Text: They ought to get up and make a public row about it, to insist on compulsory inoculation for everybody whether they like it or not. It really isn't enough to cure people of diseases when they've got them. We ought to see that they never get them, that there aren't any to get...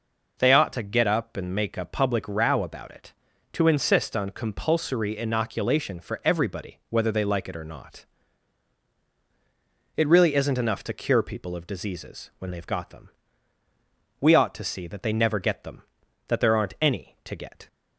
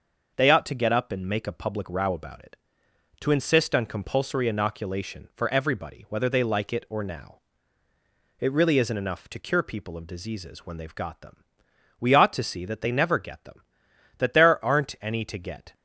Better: first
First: none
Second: starts louder than the rest; noticeable; until 1.3 s; 6 dB // says "now" for "not"; at 7.0 s

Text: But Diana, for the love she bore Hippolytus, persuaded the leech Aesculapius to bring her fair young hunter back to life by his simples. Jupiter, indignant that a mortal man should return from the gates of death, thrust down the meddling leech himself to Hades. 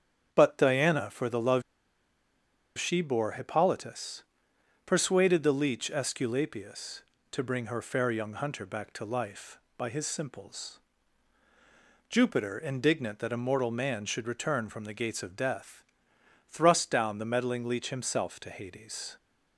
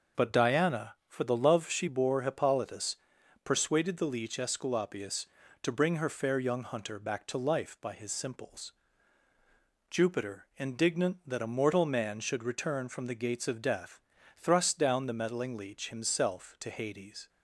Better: second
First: starts louder than the rest; strong; until 1.3 s; 8 dB // pauses between "love" and "she"; at 1.6 s; 1.1 s long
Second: none

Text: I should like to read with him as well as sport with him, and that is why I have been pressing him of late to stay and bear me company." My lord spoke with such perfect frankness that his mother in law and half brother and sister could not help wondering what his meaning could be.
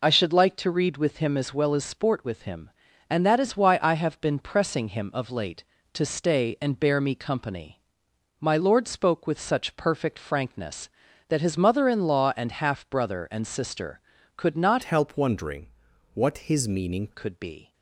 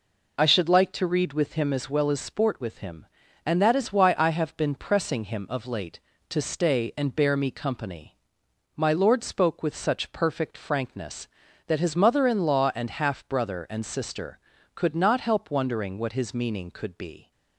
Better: second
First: changes voice from "help" to "meaning"; from 14.8 to 17.0 s; 2.2 s long // pauses between "wondering" and "what"; noticeable; at 15.6 s; 0.48 s long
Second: none

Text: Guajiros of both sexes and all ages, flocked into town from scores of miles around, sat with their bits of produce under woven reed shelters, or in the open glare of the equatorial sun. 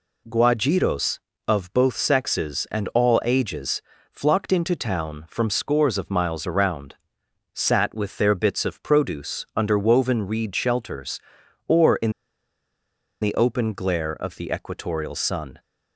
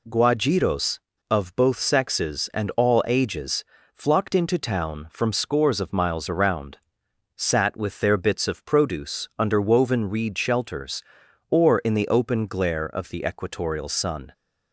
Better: second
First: pauses between "in" and "the"; at 12.1 s; 1.1 s long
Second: none

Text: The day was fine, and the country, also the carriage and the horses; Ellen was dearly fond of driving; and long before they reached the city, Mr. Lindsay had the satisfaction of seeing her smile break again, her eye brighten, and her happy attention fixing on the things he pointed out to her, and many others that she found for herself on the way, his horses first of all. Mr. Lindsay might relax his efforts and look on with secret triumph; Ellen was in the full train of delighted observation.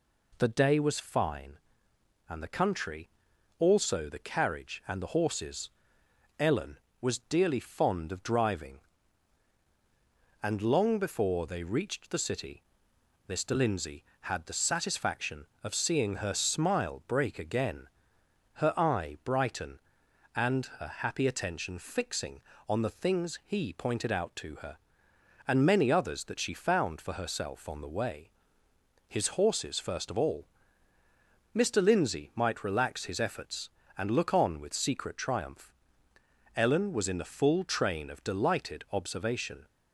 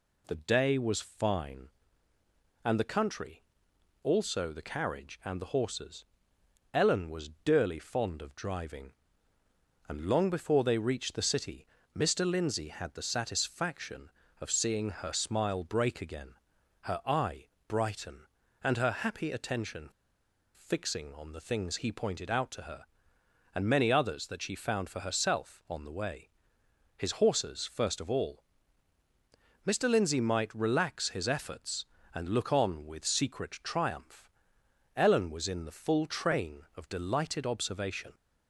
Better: first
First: none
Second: pauses between "eye" and "brighten"; slight; at 17.4 s; 0.22 s long // pauses between "attention" and "fixing"; noticeable; at 19.8 s; 0.65 s long

